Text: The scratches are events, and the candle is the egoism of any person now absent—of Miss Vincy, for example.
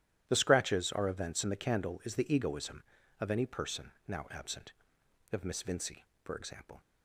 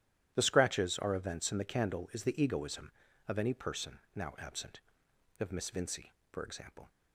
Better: neither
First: starts louder than the rest; strong; until 1.2 s; 12 dB // pauses between "person" and "now"; slight; at 3.9 s; 0.16 s long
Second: starts louder than the rest; strong; until 1.3 s; 12 dB // pauses between "person" and "now"; slight; at 3.9 s; 0.16 s long

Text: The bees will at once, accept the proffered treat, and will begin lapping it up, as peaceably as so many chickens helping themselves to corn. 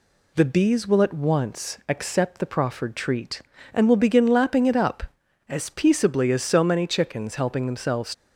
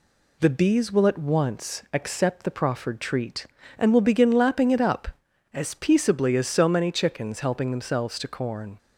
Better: second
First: stops before "to corn"; at 8.1 s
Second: none

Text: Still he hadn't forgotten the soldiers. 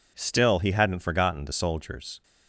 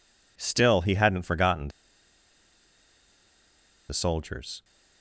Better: first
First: none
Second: pauses between "forgotten" and "the"; strong; at 1.6 s; 2.2 s long

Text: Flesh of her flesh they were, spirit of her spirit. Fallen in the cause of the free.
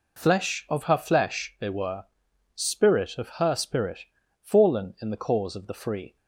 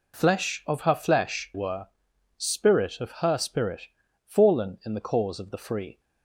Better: first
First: none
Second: skips "they"; at 1.5 s

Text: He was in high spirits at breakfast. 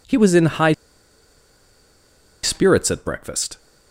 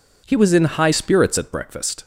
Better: second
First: pauses between "high" and "spirits"; strong; at 0.7 s; 1.7 s long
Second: none

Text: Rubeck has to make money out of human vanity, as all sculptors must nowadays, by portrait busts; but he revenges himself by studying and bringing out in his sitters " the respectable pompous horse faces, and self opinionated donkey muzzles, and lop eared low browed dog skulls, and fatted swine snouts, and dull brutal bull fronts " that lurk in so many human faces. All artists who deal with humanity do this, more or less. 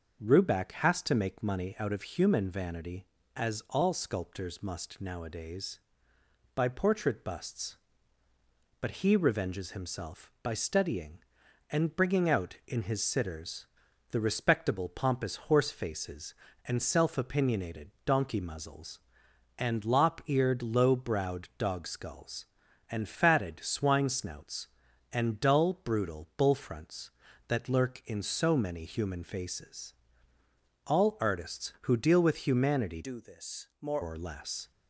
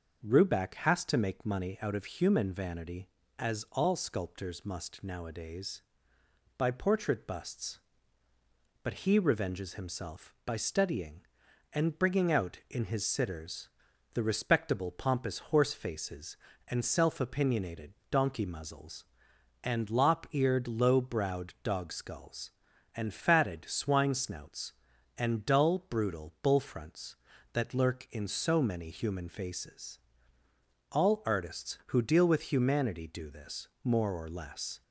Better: second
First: starts louder than the rest; until 1.2 s; 6.5 dB // pauses between "opinionated" and "donkey"; slight; at 17.9 s; 0.16 s long // changes voice from "do" to "more"; from 33.0 to 34.0 s; 1.0 s long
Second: starts louder than the rest; until 1.2 s; 6.5 dB // pauses between "opinionated" and "donkey"; slight; at 17.9 s; 0.18 s long

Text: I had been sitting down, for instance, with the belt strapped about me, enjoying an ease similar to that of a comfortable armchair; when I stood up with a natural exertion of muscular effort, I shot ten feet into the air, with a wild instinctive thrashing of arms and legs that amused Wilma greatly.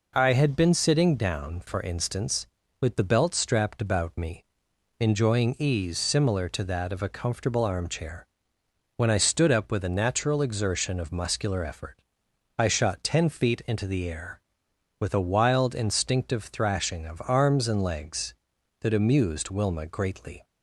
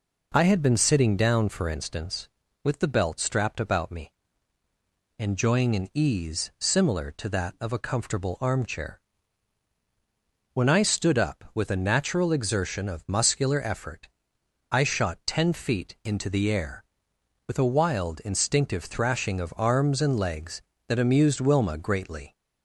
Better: second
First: skips "an"; at 5.5 s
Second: none

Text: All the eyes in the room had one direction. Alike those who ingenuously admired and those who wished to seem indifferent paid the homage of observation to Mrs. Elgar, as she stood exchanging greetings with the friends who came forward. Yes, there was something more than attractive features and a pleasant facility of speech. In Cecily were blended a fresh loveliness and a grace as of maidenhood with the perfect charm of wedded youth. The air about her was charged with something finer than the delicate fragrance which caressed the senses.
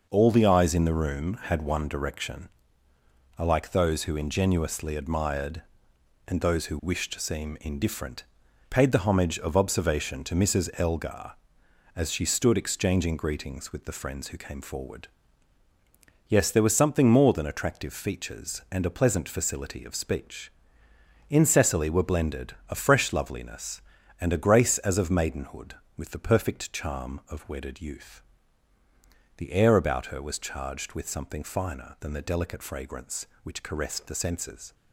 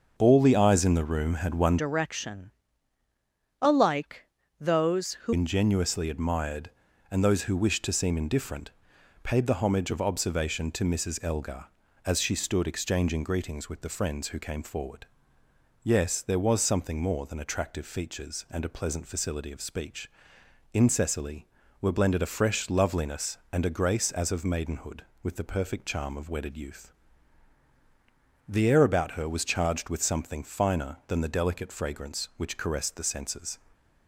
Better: first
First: pauses between "indifferent" and "paid"; noticeable; at 8.2 s; 0.46 s long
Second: starts louder than the rest; noticeable; until 1.1 s; 6 dB // changes voice from "direction" to "who"; from 1.7 to 5.3 s; 3.6 s long // pauses between "Alike" and "those"; slight; at 4.2 s; 0.34 s long // pauses between "indifferent" and "paid"; noticeable; at 8.7 s; 0.50 s long

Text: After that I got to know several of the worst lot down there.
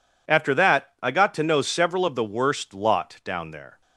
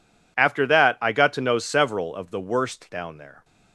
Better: first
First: none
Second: skips "lot"; at 2.8 s

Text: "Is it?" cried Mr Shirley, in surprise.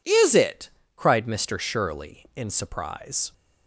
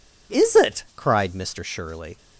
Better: first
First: none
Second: stops before "in surprise"; at 2.1 s

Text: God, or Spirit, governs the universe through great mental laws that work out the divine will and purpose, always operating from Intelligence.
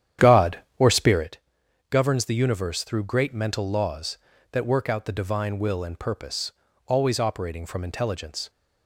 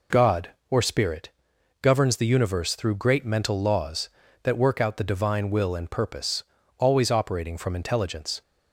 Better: second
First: starts louder than the rest; strong; until 1.3 s; 10 dB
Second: none

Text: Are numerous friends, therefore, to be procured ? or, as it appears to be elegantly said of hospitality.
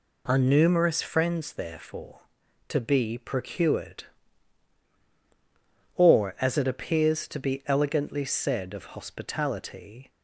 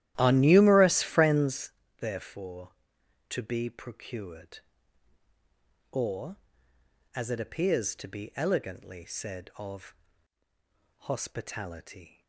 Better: first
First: none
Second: starts louder than the rest; strong; until 1.7 s; 13 dB // pauses between "of" and "hospitality"; at 9.9 s; 1.1 s long

